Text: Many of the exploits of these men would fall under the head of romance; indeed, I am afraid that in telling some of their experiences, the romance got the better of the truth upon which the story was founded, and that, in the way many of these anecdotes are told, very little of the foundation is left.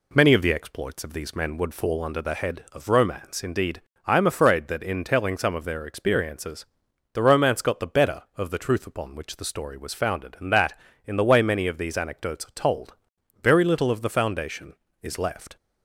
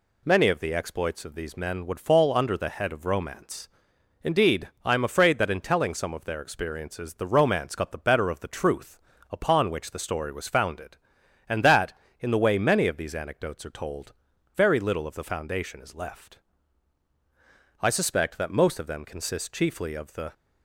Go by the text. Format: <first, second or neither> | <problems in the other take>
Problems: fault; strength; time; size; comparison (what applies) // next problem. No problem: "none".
first | pauses between "truth" and "upon"; slight; at 8.9 s; 0.32 s long // goes on to say "I suspect that most of them consist chiefly of the"; strong; from 17.8 s on; 2.5 s long